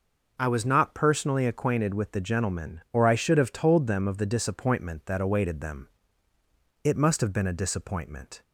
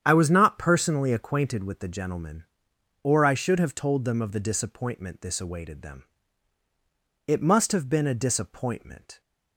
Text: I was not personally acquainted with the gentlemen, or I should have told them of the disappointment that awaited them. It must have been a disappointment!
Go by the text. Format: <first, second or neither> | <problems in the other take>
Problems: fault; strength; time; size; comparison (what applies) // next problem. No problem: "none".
first | starts louder than the rest; strong; until 1.0 s; 9 dB // says "this" for "that"; at 5.2 s